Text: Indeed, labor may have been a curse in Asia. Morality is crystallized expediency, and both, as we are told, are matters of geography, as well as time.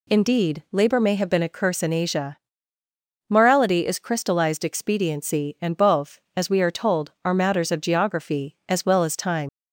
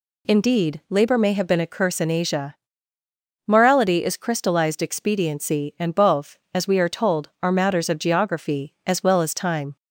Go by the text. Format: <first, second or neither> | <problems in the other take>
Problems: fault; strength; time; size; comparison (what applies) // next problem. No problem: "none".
second | leaves "time" unfinished; at 9.4 s; 95 ms